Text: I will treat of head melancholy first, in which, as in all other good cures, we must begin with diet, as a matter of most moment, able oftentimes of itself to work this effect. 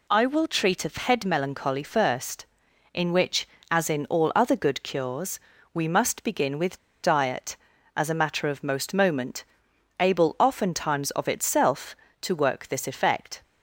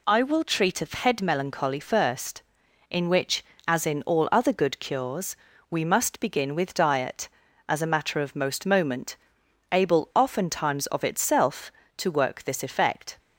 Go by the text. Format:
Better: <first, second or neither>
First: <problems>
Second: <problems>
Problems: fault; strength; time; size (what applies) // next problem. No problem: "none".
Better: second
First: pauses between "with" and "diet"; slight; at 6.7 s; 0.25 s long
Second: none